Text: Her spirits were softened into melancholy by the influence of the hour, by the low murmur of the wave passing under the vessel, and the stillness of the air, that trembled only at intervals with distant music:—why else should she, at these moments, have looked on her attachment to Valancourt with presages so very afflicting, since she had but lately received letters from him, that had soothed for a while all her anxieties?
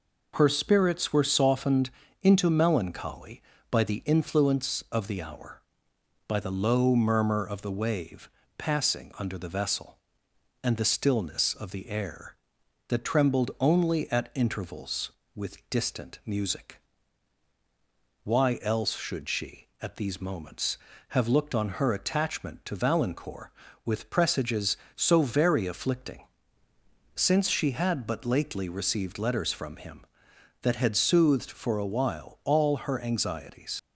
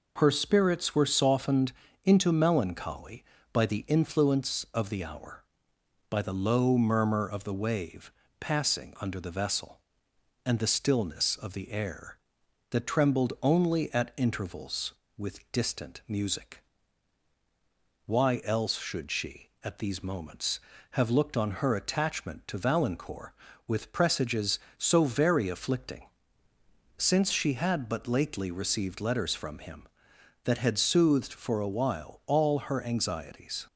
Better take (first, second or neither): second